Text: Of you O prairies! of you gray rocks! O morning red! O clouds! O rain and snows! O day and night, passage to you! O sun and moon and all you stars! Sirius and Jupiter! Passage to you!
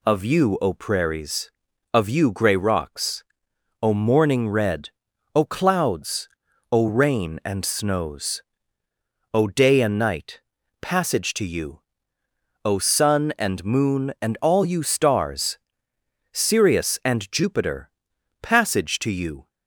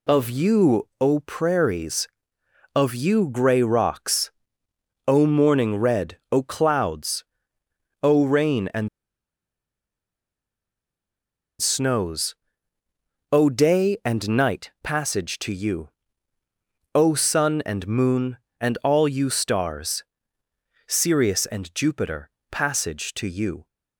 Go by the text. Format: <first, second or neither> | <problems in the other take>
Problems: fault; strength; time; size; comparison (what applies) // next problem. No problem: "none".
first | pauses between "and" and "snows"; strong; at 8.8 s; 2.7 s long